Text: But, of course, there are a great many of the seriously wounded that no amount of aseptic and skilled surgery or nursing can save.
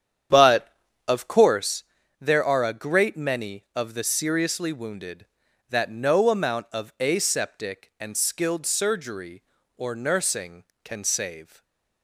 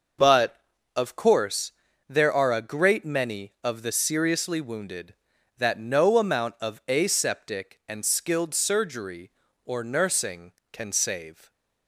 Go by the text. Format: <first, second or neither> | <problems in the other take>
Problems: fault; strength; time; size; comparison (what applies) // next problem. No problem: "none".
second | starts louder than the rest; strong; until 1.8 s; 9 dB // stays silent after the last word; slight; from 11.4 s on; 0.6 s long